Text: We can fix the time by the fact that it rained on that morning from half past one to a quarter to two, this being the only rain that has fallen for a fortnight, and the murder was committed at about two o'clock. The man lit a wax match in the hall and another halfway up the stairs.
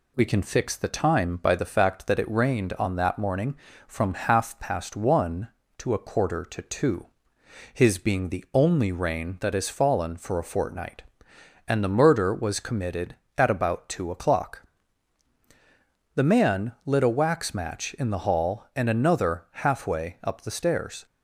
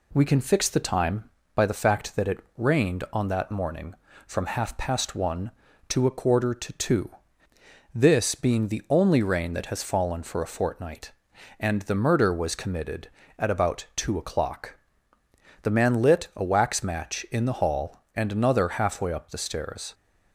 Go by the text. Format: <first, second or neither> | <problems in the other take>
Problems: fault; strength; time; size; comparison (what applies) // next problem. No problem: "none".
second | says "his" for "this"; at 7.7 s